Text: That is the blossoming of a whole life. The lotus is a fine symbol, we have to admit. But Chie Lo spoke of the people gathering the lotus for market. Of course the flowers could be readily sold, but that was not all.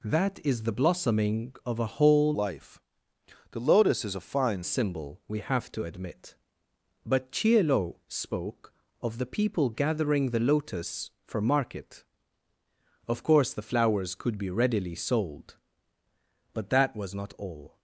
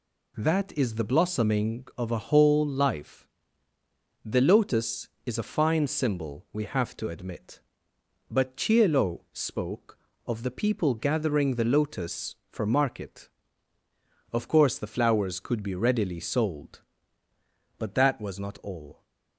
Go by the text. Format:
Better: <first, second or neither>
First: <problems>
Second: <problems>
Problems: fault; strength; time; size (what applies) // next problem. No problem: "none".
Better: second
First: changes voice from "life" to "fine"; from 2.3 to 4.6 s; 2.3 s long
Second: none